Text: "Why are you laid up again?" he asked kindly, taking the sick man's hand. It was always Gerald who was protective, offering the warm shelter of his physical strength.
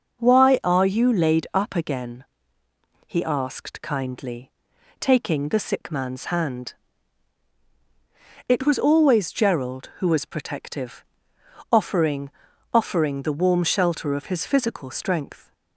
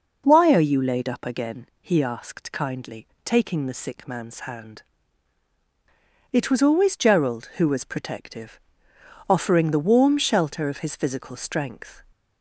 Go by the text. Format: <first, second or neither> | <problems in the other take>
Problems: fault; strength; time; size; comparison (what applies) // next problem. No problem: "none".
second | says "offering" twice; at 12.7 s